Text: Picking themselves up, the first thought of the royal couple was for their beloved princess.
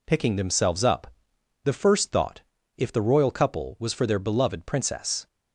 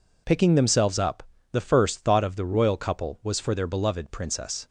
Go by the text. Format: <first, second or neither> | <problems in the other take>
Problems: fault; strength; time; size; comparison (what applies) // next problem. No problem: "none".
second | says "if" for "of"; at 2.7 s